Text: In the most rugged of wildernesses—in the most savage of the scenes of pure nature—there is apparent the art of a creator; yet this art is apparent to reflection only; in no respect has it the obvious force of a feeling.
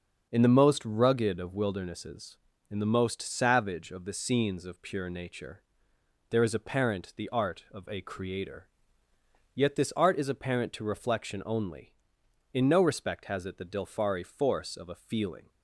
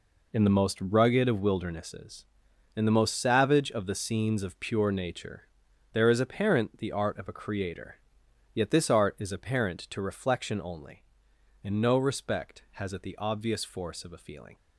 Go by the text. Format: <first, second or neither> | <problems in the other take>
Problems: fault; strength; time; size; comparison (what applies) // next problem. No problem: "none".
second | starts louder than the rest; until 1.3 s; 6.5 dB // says "dilfari" for "obvious"; at 13.6 s